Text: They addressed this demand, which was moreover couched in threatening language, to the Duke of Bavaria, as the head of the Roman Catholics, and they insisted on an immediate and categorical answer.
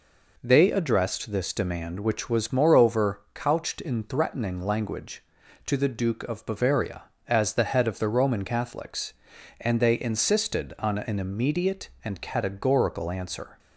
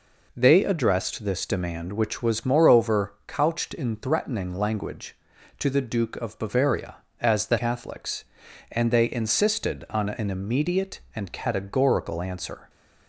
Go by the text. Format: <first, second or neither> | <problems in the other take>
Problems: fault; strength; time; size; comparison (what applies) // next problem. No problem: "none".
first | skips "head of the Roman"; at 7.5 s